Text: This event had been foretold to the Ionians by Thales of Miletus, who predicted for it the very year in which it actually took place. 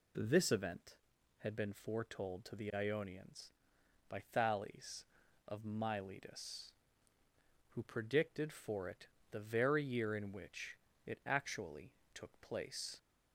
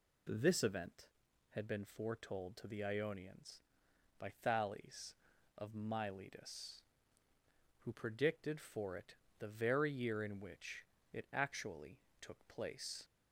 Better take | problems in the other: neither | pauses between "it" and "the"; slight; the same in both // pauses between "which" and "it"; slight; the same in both // pauses between "actually" and "took"; slight; the same in both

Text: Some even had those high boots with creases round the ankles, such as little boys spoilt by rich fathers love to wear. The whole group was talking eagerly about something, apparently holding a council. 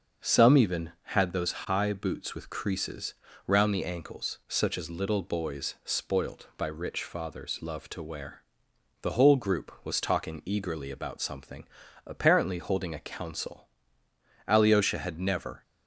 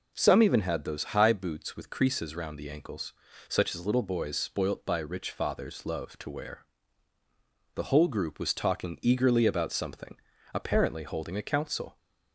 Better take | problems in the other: second | starts louder than the rest; until 1.3 s; 6 dB // pauses between "creases" and "round"; slight; at 3.1 s; 0.32 s long // goes on to say "Alyosha had never"; noticeable; from 14.4 s on; 1.1 s long

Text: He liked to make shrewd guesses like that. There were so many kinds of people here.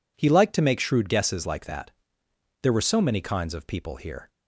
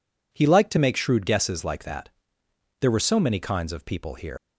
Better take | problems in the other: first | leaves "here" unfinished; at 4.3 s; 95 ms

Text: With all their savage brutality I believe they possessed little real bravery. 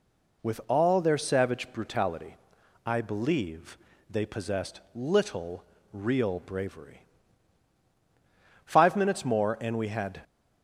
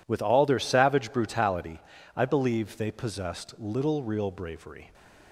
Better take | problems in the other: second | pauses between "brutality" and "I"; noticeable; at 2.3 s; 0.50 s long; slight in the second // pauses between "believe" and "they"; slight; at 3.7 s; 0.32 s long // pauses between "possessed" and "little"; slight; at 4.7 s; 0.16 s long // pauses between "little" and "real"; slight; at 5.6 s; 0.30 s long // goes on to say "Five minutes more and we had"; from 8.6 s on; 1.5 s long

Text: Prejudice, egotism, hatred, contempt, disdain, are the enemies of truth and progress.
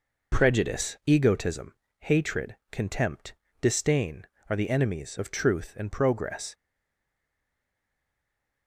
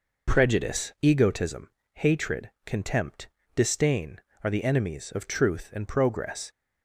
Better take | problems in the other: second | stays silent after the last word; from 6.5 s on; 2.1 s long

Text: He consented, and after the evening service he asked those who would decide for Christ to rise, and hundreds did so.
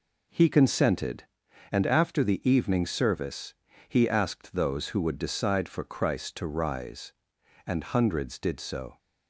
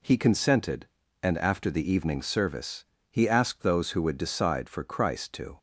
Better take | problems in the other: first | pauses between "service" and "he"; slight; at 2.8 s; 0.28 s long; slight in the first // stops before "rise and hundreds did so"; at 5.5 s

